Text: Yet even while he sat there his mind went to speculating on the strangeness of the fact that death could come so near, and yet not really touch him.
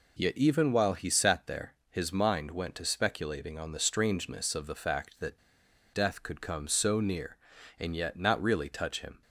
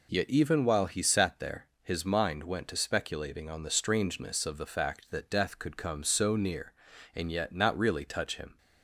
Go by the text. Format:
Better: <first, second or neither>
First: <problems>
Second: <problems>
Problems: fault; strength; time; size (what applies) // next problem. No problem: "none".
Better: second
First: pauses between "there" and "his"; slight; at 1.7 s; 0.18 s long // pauses between "that" and "death"; noticeable; at 5.3 s; 0.54 s long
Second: pauses between "there" and "his"; slight; at 1.6 s; 0.18 s long